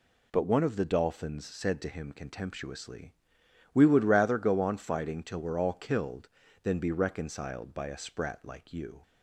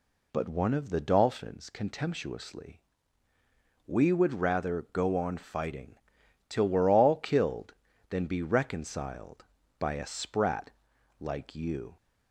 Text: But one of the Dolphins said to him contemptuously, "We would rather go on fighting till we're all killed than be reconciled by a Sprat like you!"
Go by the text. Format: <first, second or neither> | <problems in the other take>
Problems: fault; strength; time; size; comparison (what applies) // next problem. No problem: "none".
first | skips "said to him"; at 1.7 s // pauses between "fighting" and "till"; noticeable; at 5.9 s; 0.54 s long // pauses between "Sprat" and "like"; noticeable; at 10.7 s; 0.48 s long